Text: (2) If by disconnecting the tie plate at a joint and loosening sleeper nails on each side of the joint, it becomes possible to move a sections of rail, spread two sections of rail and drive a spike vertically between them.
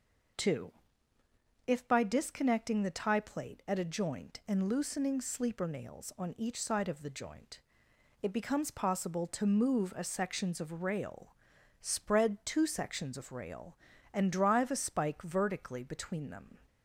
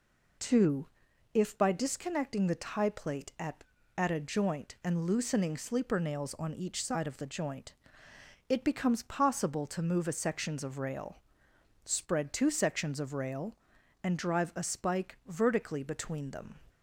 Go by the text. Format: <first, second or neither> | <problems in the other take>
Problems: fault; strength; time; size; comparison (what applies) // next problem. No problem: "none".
first | says "at" twice; at 3.9 s